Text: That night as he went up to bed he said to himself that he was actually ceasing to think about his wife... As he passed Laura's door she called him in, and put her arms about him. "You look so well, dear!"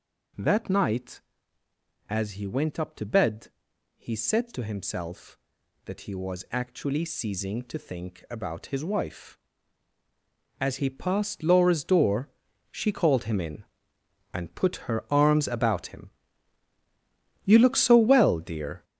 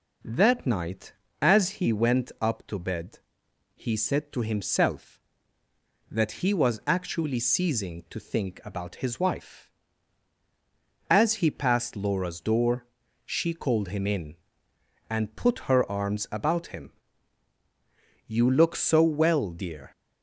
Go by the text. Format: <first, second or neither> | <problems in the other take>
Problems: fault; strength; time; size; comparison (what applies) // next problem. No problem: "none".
second | gets louder; strong; throughout; 8 dB // pauses between "bed" and "he"; noticeable; at 3.4 s; 0.50 s long; noticeable in the second // pauses between "door" and "she"; at 12.2 s; 0.42 s long; also in the second